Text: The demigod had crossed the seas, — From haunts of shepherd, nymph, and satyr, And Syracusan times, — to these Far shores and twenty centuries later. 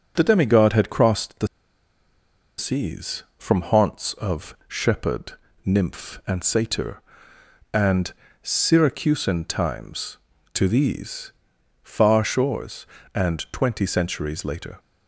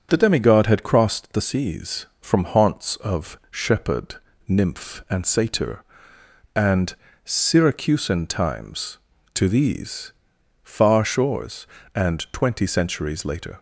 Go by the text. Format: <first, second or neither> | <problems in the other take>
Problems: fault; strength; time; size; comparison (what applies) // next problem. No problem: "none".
second | starts louder than the rest; until 1.1 s; 7 dB; also in the second // pauses between "the" and "seas"; at 1.4 s; 1.1 s long // pauses between "And" and "Syracusan"; slight; at 8.1 s; 0.30 s long; slight in the second // pauses between "these" and "Far"; noticeable; at 11.3 s; 0.50 s long; noticeable in the second